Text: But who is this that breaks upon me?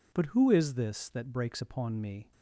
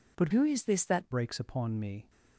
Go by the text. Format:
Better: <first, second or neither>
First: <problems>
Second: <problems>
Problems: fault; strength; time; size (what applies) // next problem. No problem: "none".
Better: first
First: none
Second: changes voice from "who" to "that"; from 0.3 to 1.1 s; 0.8 s long